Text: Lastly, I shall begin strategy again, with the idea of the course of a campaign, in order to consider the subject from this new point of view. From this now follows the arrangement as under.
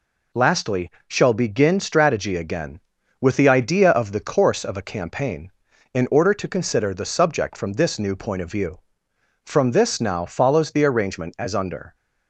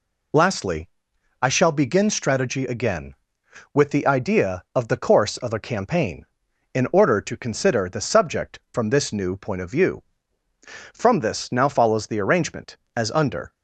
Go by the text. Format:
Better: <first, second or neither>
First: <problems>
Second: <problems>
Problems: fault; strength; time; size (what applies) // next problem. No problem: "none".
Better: second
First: skips "I"; at 0.9 s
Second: none